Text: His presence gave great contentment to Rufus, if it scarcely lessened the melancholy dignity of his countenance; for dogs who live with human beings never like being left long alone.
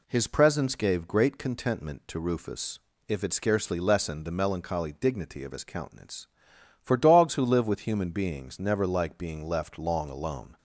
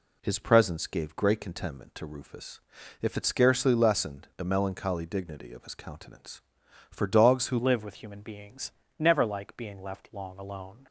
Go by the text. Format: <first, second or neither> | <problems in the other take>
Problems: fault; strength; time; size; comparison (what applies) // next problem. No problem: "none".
first | changes voice at "live"; from 7.5 s on; 3.3 s long // pauses between "beings" and "never"; slight; at 8.7 s; 0.26 s long